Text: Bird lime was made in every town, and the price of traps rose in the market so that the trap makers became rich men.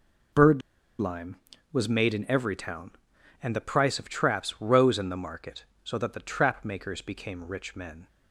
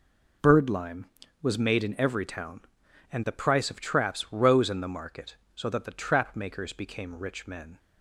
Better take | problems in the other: second | pauses between "Bird" and "lime"; at 0.6 s; 0.40 s long

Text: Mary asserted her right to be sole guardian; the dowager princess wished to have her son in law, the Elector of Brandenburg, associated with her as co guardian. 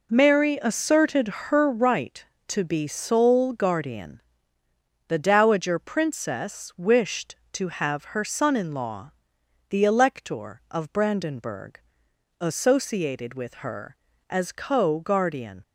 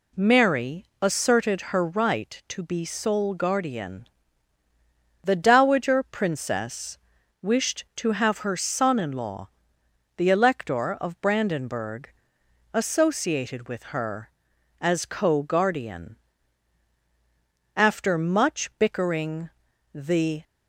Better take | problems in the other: first | pauses between "Mary" and "asserted"; slight; at 0.8 s; 0.16 s long // pauses between "princess" and "wished"; at 6.9 s; 0.42 s long // goes on to say "After much bickering the"; strong; from 17.7 s on; 2.6 s long

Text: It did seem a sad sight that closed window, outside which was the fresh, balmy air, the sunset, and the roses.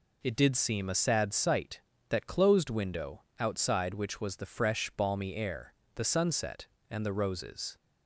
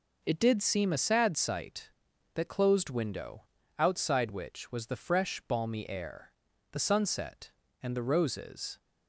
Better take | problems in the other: neither | none

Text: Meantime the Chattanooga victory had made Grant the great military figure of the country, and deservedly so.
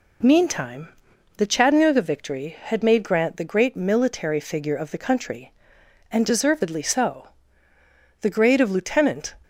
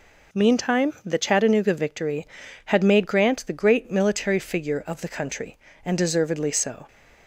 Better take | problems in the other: second | pauses between "Meantime" and "the"; noticeable; at 0.8 s; 0.50 s long // goes on to say "The grade of lieutenant"; noticeable; from 8.2 s on; 1.1 s long

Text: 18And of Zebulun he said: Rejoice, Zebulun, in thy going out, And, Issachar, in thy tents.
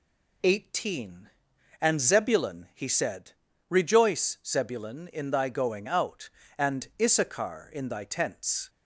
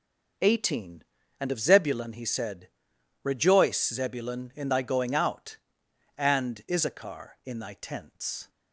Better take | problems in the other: second | skips "of"; at 1.9 s

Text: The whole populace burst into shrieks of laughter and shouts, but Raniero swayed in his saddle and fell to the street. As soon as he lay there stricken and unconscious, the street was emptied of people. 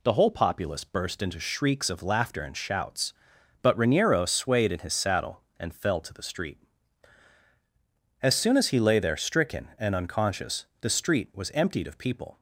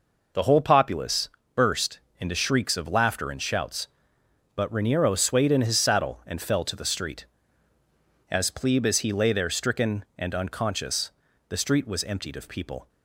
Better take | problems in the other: first | pauses between "populace" and "burst"; slight; at 1.3 s; 0.24 s long // pauses between "burst" and "into"; slight; at 2.0 s; 0.20 s long // says "plebe" for "soon"; at 8.5 s

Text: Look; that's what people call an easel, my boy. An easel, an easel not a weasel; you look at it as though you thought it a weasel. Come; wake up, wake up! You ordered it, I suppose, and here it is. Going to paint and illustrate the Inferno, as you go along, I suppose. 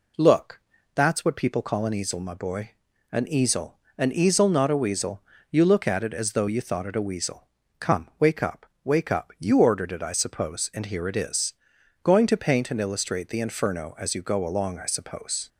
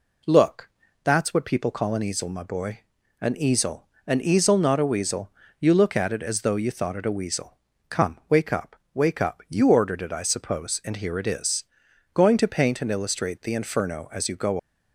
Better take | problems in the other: first | stops before "along I suppose"; at 14.5 s

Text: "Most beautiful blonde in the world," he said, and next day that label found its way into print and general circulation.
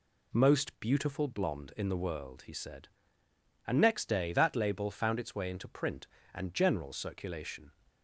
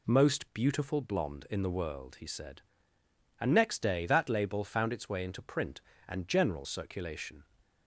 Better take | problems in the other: neither | none

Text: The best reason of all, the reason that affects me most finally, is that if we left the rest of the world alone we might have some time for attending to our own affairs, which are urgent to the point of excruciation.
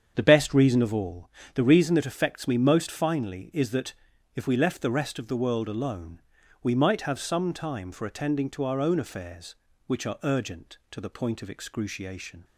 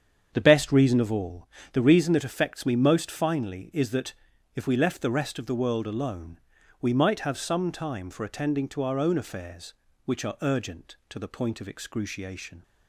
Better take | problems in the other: neither | starts louder than the rest; strong; the same in both // pauses between "that" and "if"; the same in both // pauses between "alone" and "we"; the same in both

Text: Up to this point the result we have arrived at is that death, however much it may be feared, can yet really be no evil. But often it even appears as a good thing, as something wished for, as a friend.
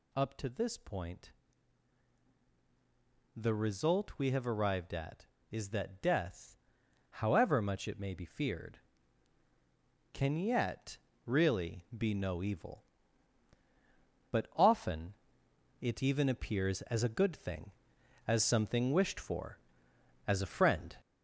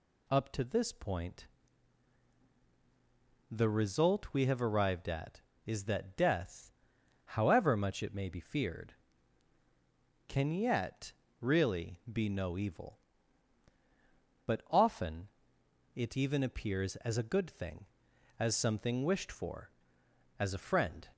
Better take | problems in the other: second | gets louder; noticeable; throughout; 5.5 dB // pauses between "point" and "the"; strong; at 1.3 s; 2.0 s long; strong in the second // pauses between "yet" and "really"; slight; at 10.9 s; 0.28 s long; slight in the second // pauses between "often" and "it"; noticeable; at 15.1 s; 0.66 s long; noticeable in the second

